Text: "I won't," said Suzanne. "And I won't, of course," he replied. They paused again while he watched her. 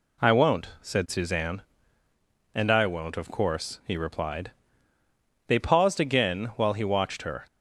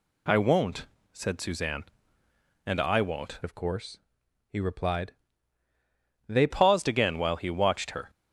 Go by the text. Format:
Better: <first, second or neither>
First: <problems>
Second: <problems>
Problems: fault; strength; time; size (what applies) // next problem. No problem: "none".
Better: first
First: none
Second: changes voice from "of" to "They"; from 3.4 to 6.4 s; 3.0 s long